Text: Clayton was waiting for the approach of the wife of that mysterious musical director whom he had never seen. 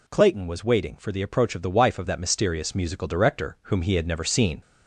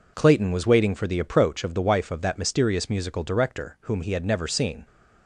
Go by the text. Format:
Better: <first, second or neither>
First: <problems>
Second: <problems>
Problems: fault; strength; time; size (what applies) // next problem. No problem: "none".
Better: second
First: gets louder; slight; throughout; 2 dB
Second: none